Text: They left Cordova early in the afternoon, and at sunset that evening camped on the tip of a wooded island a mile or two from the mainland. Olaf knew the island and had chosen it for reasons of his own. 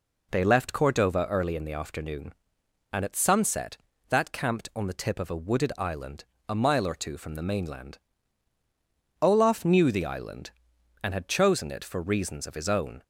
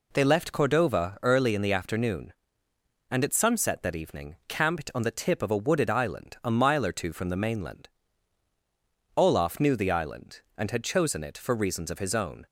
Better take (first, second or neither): second